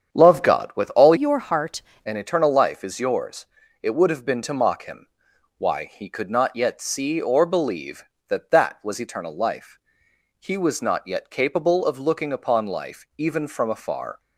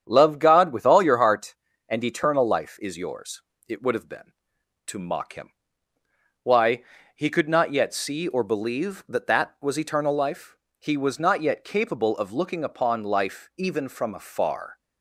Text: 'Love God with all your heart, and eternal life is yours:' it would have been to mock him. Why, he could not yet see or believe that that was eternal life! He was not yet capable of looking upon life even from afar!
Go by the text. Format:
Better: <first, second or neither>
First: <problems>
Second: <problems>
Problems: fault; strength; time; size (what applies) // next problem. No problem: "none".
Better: second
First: starts louder than the rest; strong; until 1.2 s; 8 dB // changes voice from "your" to "heart"; from 1.1 to 1.8 s; 0.7 s long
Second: starts louder than the rest; strong; until 1.0 s; 8.5 dB